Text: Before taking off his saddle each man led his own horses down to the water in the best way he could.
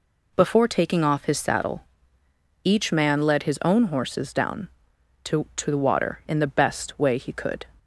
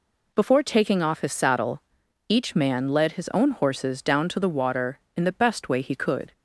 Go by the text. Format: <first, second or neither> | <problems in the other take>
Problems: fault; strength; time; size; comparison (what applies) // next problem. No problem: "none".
second | pauses between "saddle" and "each"; noticeable; at 1.8 s; 0.82 s long; noticeable in the second // says "to" twice; at 5.5 s